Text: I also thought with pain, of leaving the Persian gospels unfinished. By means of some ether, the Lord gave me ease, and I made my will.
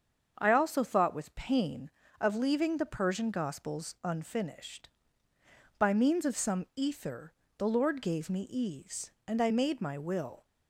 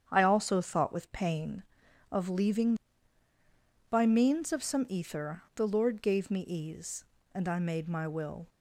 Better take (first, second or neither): first